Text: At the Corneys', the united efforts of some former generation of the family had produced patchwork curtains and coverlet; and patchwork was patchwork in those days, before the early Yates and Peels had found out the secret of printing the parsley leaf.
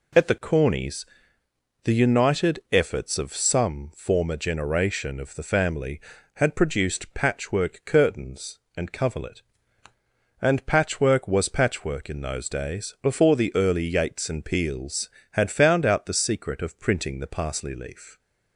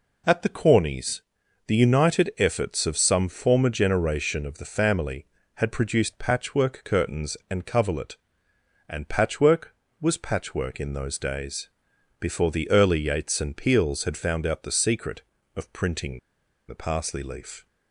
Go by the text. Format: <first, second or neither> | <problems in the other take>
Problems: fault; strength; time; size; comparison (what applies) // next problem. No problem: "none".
first | pauses between "printing" and "the"; noticeable; at 16.1 s; 0.48 s long